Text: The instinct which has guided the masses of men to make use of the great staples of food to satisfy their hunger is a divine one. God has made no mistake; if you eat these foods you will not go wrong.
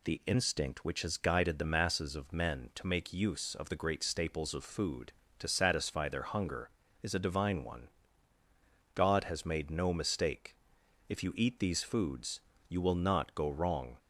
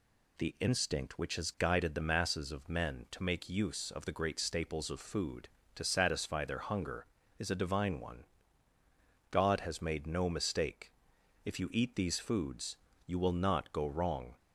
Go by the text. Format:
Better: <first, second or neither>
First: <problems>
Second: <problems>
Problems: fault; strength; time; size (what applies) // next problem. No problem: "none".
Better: neither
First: pauses between "foods" and "you"; slight; at 12.4 s; 0.28 s long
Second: pauses between "foods" and "you"; slight; at 12.7 s; 0.30 s long